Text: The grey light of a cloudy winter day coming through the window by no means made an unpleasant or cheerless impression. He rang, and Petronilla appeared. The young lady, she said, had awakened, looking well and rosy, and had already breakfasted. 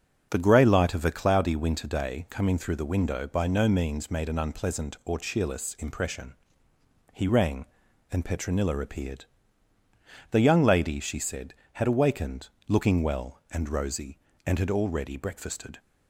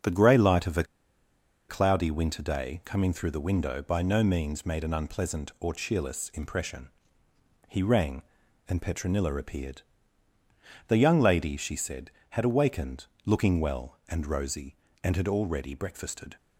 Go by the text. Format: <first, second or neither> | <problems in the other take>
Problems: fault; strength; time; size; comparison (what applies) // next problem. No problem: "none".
first | starts louder than the rest; until 1.9 s; 6.5 dB; also in the first // pauses between "a" and "cloudy"; noticeable; at 0.8 s; 0.85 s long